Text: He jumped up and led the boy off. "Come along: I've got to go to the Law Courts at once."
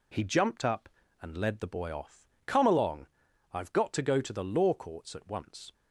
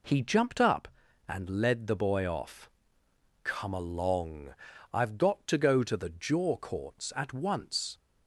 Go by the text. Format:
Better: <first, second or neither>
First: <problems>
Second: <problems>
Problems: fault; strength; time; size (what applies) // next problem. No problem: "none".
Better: first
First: none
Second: says "Jaw" for "Law"; at 6.1 s